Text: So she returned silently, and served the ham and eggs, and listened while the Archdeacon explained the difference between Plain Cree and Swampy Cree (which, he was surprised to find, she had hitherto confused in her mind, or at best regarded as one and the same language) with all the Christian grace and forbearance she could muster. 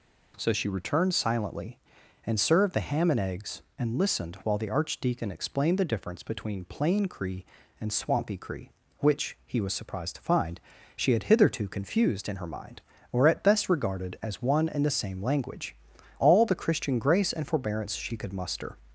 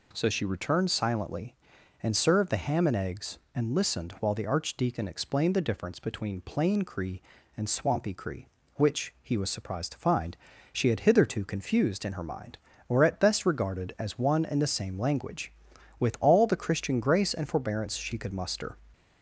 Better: second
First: skips "with"; at 15.9 s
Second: none

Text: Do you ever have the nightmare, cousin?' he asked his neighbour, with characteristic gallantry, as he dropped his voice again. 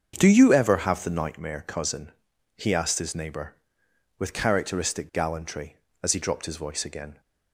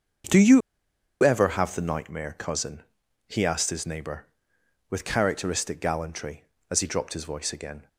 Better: first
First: starts louder than the rest; until 1.1 s; 7 dB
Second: starts louder than the rest; until 1.9 s; 6.5 dB // pauses between "you" and "ever"; noticeable; at 0.6 s; 0.63 s long

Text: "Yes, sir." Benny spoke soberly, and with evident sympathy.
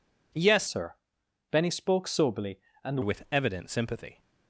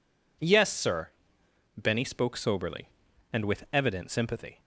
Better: second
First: changes voice from "sir" to "and"; from 0.6 to 3.0 s; 2.4 s long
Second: none

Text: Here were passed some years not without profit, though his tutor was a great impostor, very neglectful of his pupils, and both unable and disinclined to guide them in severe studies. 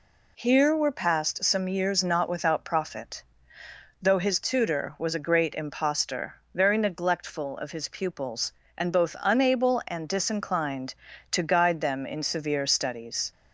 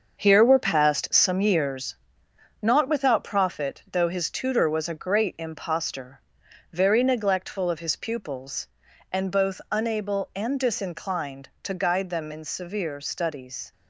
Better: first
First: none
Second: gets quieter; strong; throughout; 8.5 dB // pauses between "years" and "not"; noticeable; at 1.9 s; 0.66 s long

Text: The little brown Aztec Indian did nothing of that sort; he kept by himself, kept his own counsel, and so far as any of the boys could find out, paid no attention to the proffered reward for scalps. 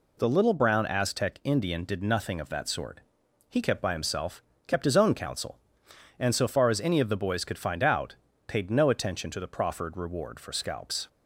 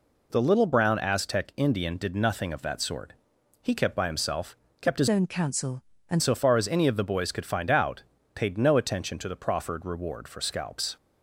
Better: first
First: none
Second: changes voice from "own" to "and"; from 5.0 to 6.2 s; 1.2 s long

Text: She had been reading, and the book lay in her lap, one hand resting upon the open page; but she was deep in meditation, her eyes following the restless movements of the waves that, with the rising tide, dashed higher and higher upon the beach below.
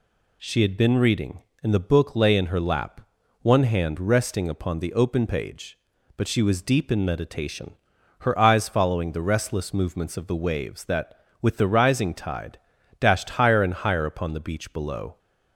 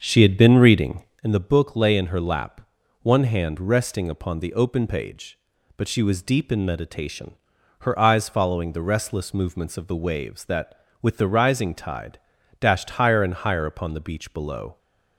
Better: first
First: none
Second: starts louder than the rest; until 1.3 s; 6.5 dB

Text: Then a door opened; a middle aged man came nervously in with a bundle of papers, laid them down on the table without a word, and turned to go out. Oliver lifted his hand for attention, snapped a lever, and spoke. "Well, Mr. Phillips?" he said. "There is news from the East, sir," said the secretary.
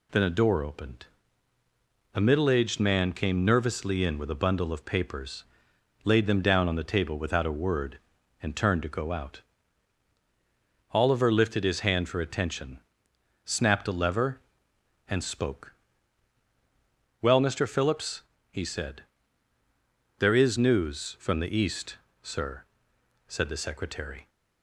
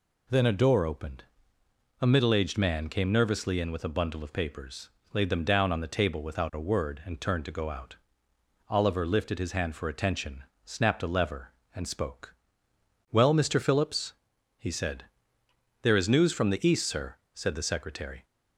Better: neither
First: none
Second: none

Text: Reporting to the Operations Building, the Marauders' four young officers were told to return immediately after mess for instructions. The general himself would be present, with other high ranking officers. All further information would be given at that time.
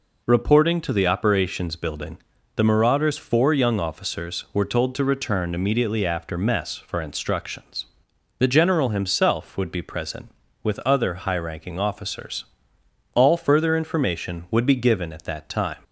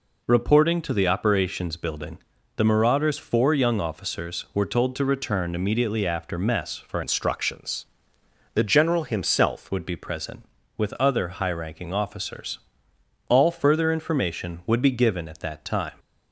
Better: first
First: none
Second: changes voice from "instructions" to "himself"; from 7.0 to 9.6 s; 2.6 s long

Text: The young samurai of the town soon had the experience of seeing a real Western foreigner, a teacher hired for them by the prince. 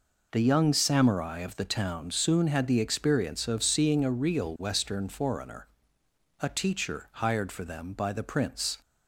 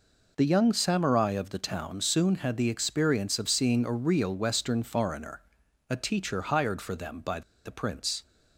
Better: first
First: none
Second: pauses between "by" and "the"; slight; at 7.4 s; 0.24 s long

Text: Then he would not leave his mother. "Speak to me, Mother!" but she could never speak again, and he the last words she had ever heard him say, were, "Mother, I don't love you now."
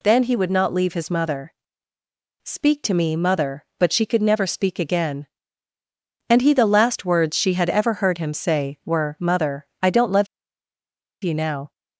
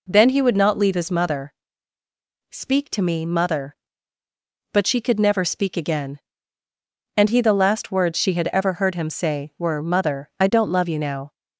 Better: second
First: pauses between "love" and "you"; noticeable; at 10.2 s; 0.97 s long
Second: none

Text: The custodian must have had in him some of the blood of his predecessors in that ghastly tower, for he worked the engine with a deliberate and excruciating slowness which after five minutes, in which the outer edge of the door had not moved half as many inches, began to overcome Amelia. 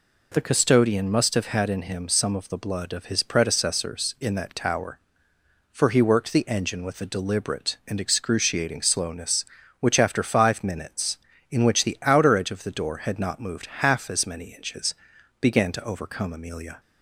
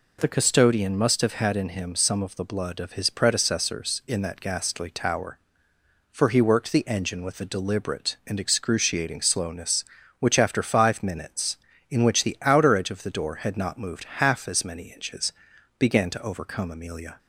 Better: second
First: skips "ghastly"; at 4.5 s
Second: none

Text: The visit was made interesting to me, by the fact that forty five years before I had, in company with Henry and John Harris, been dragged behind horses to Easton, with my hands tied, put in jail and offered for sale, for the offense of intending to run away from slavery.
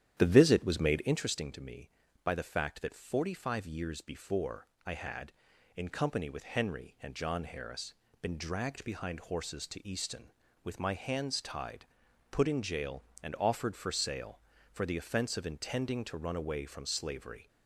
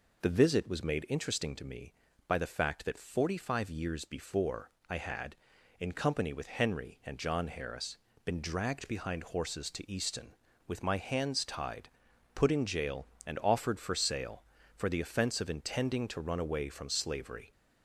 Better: second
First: starts louder than the rest; strong; until 1.4 s; 10.5 dB // pauses between "before" and "I"; slight; at 4.6 s; 0.18 s long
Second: pauses between "before" and "I"; slight; at 4.6 s; 0.18 s long

